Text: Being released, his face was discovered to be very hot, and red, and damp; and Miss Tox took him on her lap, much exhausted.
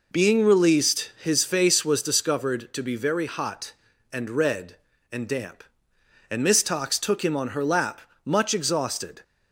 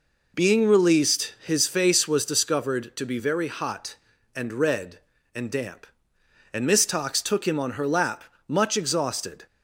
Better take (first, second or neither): neither